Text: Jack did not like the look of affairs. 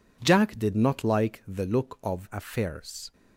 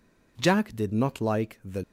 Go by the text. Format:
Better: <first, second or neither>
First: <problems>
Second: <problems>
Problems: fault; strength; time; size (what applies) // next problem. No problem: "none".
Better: first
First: none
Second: stops before "look of affairs"; at 1.8 s